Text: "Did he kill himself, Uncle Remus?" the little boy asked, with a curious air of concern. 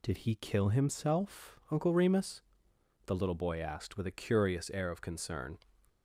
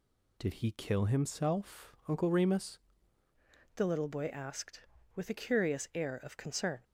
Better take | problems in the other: first | changes voice at "the"; from 3.7 s on; 3.1 s long

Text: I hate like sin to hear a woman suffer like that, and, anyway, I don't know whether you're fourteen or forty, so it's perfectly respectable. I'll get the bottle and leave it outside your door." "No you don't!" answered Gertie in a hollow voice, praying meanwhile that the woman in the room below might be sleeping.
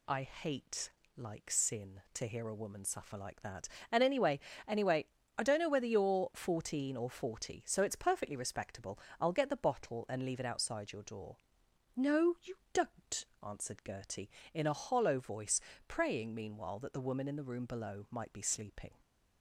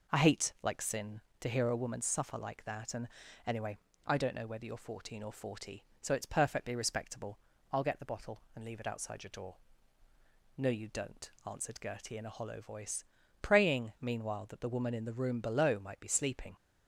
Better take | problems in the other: second | pauses between "hate" and "like"; slight; at 0.8 s; 0.28 s long // says "anyway" twice; at 4.6 s // pauses between "you" and "don't"; slight; at 12.5 s; 0.18 s long

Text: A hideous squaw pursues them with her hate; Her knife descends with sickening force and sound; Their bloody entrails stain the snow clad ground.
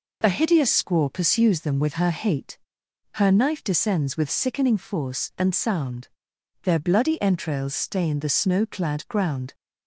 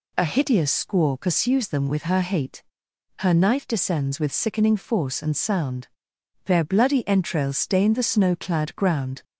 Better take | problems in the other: neither | none

